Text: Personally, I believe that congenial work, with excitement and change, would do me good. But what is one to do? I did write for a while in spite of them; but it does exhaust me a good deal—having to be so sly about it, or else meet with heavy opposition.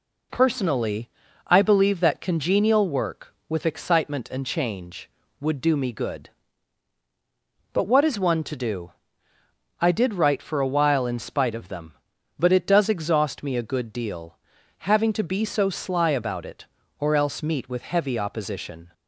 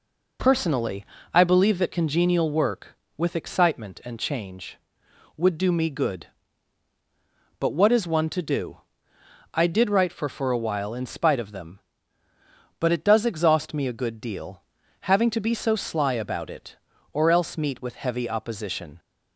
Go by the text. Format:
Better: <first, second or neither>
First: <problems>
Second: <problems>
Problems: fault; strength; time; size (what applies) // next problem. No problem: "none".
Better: first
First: none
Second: says "for" twice; at 10.2 s